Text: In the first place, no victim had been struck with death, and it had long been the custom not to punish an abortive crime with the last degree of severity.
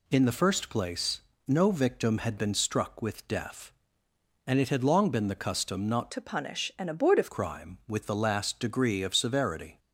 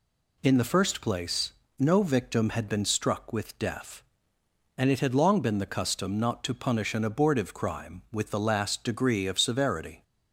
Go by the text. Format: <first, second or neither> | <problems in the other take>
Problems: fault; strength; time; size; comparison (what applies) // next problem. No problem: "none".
second | changes voice from "to" to "abortive"; from 6.1 to 7.3 s; 1.2 s long